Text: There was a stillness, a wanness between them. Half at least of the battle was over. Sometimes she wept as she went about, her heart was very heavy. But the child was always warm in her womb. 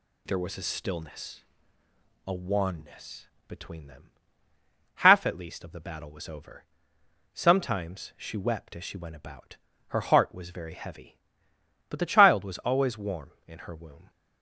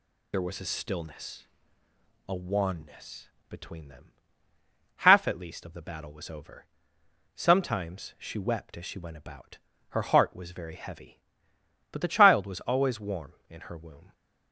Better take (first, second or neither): first